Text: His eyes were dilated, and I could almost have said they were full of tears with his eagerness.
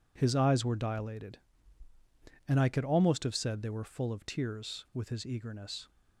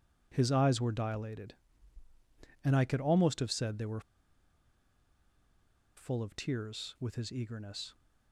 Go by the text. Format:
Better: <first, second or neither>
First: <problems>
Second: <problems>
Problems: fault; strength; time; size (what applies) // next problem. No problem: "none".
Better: first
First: none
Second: pauses between "were" and "full"; strong; at 4.0 s; 1.9 s long